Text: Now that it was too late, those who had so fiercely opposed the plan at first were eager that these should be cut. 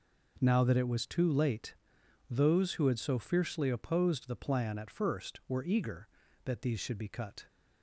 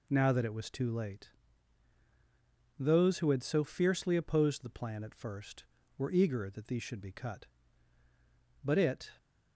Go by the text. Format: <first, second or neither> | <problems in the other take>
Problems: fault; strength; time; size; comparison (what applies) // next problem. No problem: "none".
first | goes on to say "But it"; slight; from 8.6 s on; 0.48 s long